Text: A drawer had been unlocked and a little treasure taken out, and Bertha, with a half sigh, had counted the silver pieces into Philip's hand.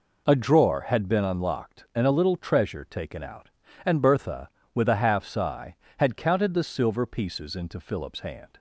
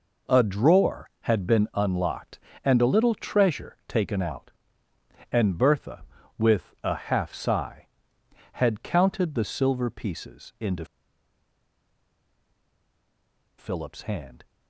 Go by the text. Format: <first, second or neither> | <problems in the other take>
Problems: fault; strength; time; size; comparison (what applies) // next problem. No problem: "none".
first | pauses between "into" and "Philip's"; strong; at 10.8 s; 2.7 s long